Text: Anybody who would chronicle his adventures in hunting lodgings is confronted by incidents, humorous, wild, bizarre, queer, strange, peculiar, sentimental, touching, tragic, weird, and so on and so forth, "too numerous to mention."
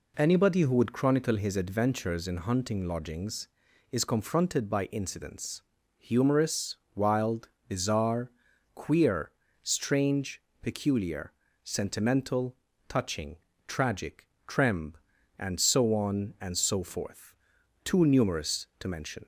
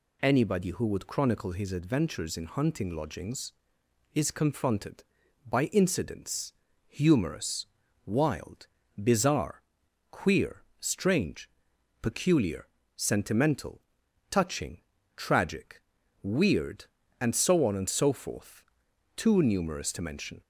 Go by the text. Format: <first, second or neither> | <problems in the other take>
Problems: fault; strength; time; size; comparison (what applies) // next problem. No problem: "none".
second | says "tremb" for "weird"; at 14.4 s